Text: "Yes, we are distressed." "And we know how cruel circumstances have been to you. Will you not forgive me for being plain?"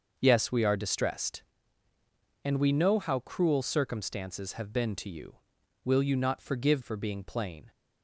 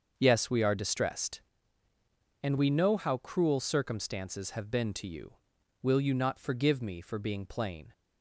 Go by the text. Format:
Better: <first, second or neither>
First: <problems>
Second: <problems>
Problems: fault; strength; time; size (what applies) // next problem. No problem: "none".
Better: second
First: starts louder than the rest; until 1.2 s; 6.5 dB // skips "me"; at 6.8 s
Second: starts louder than the rest; until 1.1 s; 6.5 dB